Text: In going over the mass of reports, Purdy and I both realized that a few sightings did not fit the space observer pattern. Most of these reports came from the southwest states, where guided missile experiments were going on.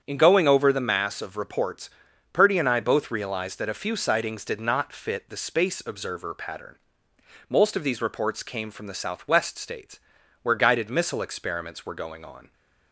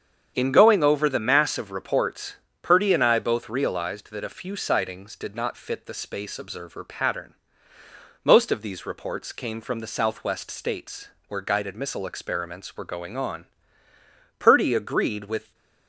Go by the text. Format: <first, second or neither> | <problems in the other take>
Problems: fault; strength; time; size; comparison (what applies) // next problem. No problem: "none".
first | starts louder than the rest; strong; until 1.3 s; 8 dB; strong in the first // goes on to say "Purdy agreed with"; noticeable; from 14.3 s on; 1.1 s long